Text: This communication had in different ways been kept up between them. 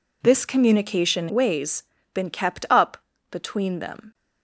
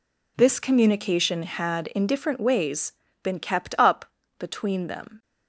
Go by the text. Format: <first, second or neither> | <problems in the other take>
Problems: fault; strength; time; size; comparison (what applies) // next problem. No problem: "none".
second | skips "had in different"; at 1.2 s // pauses between "ways" and "been"; slight; at 1.8 s; 0.30 s long; slight in the second // pauses between "up" and "between"; slight; at 2.9 s; 0.32 s long; slight in the second